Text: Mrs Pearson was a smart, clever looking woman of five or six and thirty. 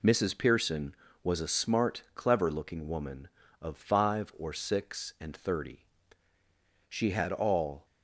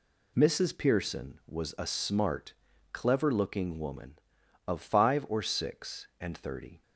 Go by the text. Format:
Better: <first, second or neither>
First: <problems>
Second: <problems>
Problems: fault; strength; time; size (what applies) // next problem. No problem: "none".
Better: second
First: goes on to say "She had all"; noticeable; from 6.8 s on; 0.96 s long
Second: none